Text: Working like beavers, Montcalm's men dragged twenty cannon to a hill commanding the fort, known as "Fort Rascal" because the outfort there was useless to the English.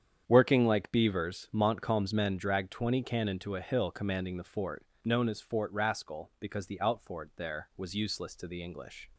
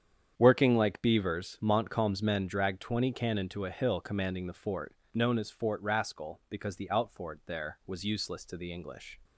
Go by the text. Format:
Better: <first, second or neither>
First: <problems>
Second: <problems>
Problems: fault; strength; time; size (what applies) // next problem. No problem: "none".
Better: neither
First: starts louder than the rest; strong; until 1.2 s; 8 dB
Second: starts louder than the rest; strong; until 1.3 s; 8 dB